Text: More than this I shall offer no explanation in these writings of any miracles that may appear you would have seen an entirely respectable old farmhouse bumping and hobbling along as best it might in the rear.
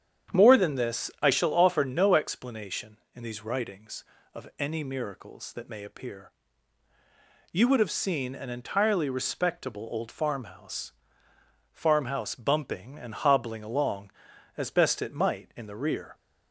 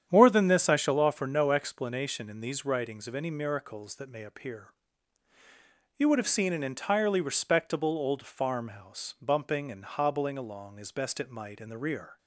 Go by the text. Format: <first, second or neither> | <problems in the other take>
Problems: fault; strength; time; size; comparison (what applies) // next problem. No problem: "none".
second | starts louder than the rest; strong; until 1.4 s; 8.5 dB; strong in the second // pauses between "appear" and "you"; at 6.3 s; 1.2 s long; strong in the second // says "farmhouse" twice; at 11.7 s